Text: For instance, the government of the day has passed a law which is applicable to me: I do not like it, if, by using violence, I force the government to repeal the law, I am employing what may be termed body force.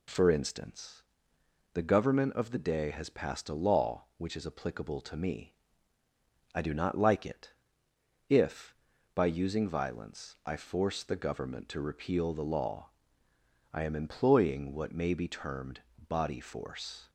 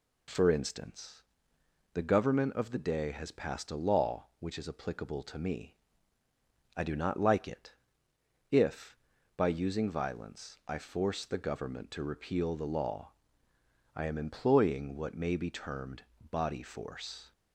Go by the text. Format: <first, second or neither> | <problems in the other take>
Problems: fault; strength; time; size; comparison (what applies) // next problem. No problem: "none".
neither | pauses between "termed" and "body"; slight; the same in both